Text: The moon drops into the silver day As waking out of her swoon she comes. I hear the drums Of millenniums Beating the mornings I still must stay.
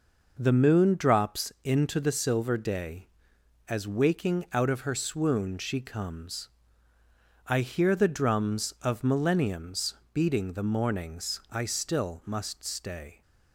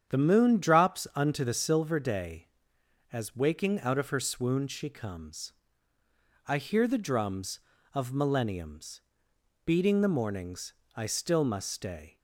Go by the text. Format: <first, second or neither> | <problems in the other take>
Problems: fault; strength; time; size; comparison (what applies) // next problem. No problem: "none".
first | starts louder than the rest; strong; until 1.1 s; 8.5 dB // says "unto" for "into"; at 1.1 s // pauses between "millenniums" and "Beating"; noticeable; at 9.0 s; 0.64 s long; slight in the first // pauses between "mornings" and "I"; slight; at 10.7 s; 0.20 s long